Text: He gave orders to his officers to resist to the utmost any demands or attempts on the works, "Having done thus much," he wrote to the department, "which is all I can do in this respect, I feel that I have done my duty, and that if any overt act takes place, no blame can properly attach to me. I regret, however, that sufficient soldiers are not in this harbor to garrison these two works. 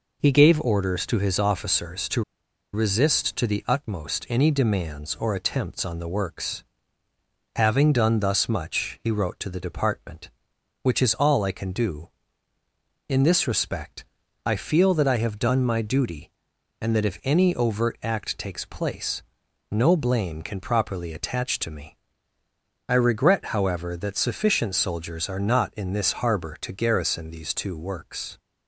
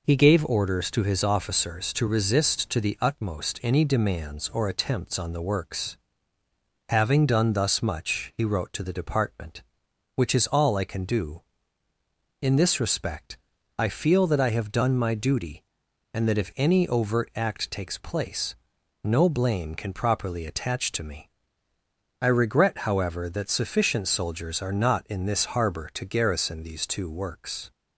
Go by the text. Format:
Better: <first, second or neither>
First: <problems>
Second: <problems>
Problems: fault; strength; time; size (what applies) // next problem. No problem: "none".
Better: second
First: pauses between "to" and "resist"; noticeable; at 2.2 s; 0.52 s long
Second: none